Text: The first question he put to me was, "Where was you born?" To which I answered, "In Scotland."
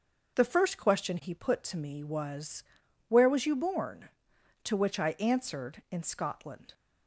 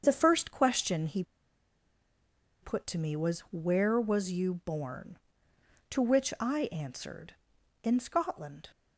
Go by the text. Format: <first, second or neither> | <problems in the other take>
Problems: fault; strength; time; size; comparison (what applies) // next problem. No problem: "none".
first | starts louder than the rest; until 1.0 s; 7 dB; noticeable in the first // pauses between "he" and "put"; strong; at 1.2 s; 1.3 s long